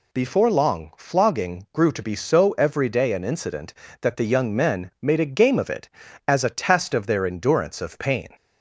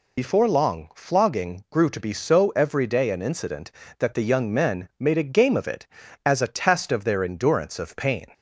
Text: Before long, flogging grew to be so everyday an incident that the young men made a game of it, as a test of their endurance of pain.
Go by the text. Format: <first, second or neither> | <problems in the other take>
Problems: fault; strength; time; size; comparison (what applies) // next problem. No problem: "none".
first | loses the start of "Before"; at 0.1 s; 70 ms